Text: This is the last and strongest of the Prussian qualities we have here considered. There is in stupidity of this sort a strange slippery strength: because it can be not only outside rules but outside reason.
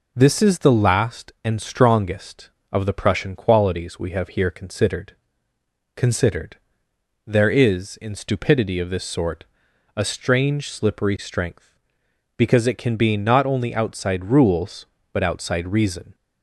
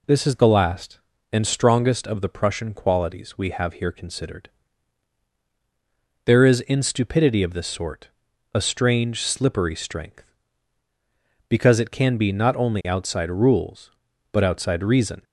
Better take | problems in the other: second | says "considered" twice; at 5.9 s // pauses between "sort" and "a"; noticeable; at 9.4 s; 0.52 s long; also in the second

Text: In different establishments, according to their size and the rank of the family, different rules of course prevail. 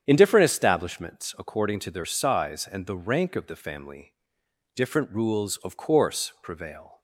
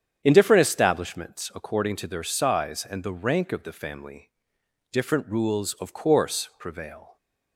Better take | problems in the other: neither | starts louder than the rest; strong; the same in both

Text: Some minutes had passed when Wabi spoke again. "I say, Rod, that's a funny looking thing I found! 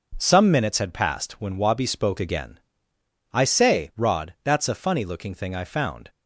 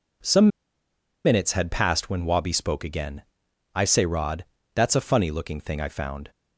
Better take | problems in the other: first | pauses between "Some" and "minutes"; noticeable; at 0.4 s; 0.77 s long

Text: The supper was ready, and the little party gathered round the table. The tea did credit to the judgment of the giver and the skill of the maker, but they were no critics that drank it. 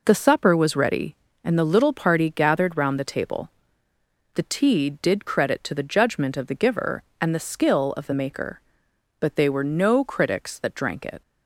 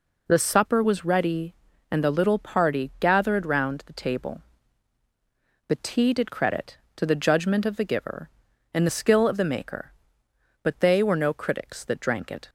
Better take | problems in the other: neither | none

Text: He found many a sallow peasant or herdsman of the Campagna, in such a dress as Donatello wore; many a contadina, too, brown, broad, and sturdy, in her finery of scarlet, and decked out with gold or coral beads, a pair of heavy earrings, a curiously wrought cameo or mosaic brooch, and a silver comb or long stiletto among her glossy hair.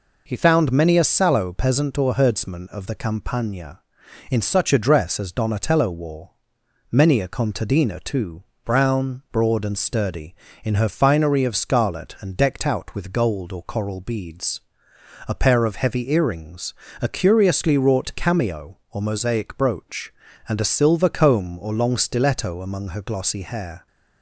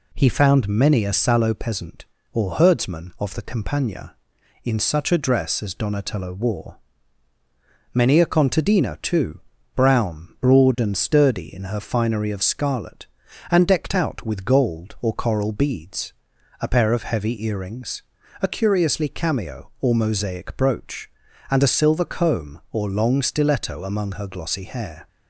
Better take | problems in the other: first | skips "wrought"; at 19.0 s

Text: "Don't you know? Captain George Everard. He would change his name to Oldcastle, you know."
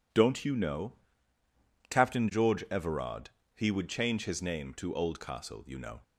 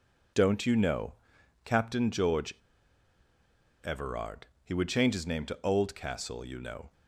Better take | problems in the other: first | pauses between "George" and "Everard"; strong; at 2.5 s; 1.3 s long

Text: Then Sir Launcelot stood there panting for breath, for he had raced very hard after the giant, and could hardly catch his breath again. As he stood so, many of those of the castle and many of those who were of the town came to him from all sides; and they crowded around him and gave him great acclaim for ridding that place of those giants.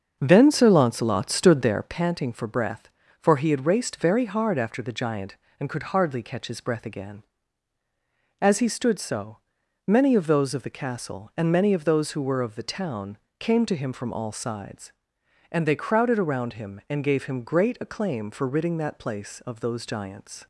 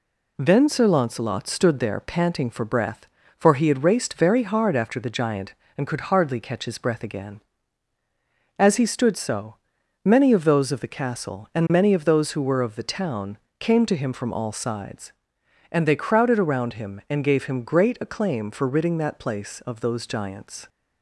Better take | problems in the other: second | starts louder than the rest; until 1.9 s; 6.5 dB // pauses between "town" and "came"; slight; at 13.1 s; 0.20 s long; slight in the second

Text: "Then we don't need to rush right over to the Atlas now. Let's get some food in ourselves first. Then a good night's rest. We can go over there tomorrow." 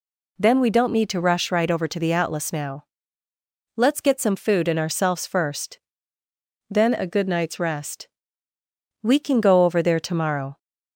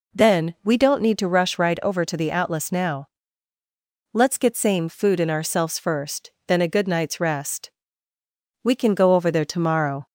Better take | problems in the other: first | says "same" for "some"; at 4.5 s

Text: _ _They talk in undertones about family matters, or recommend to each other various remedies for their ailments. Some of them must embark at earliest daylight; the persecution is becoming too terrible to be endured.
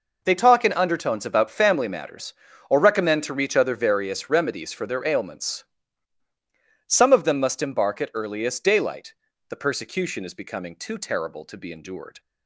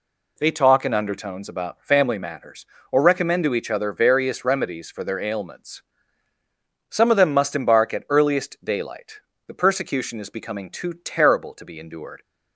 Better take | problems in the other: second | says "reach" for "each"; at 3.3 s

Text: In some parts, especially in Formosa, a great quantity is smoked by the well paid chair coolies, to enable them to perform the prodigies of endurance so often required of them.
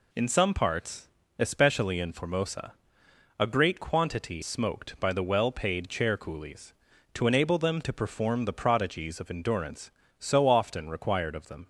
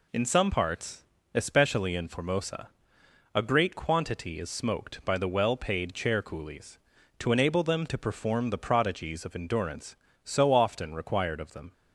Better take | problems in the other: second | skips "is"; at 4.4 s

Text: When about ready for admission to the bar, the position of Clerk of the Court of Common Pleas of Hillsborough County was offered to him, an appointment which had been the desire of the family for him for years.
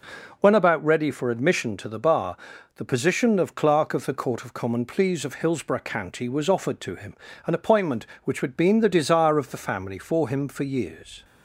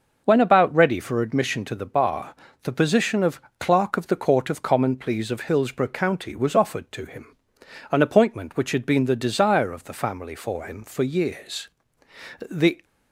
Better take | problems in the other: first | starts louder than the rest; noticeable; until 1.2 s; 6 dB // pauses between "of" and "Clerk"; slight; at 3.4 s; 0.18 s long // goes on to say "The"; slight; from 12.4 s on; 0.34 s long

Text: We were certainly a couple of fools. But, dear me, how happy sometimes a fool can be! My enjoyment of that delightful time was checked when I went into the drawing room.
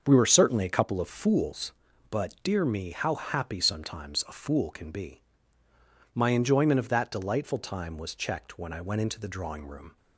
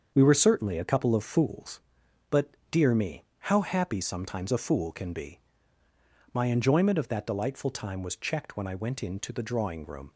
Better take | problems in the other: neither | starts louder than the rest; the same in both

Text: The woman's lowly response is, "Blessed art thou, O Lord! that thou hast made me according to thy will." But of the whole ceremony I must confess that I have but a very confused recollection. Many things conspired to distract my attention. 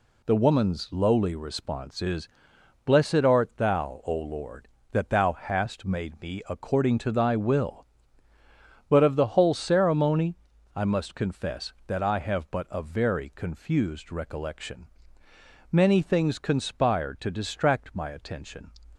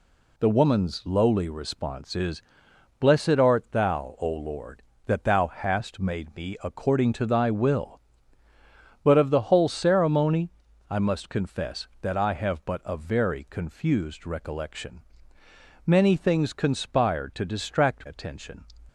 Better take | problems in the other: first | pauses between "ceremony" and "I"; at 10.4 s; 0.40 s long; also in the first // skips "my"; at 18.0 s

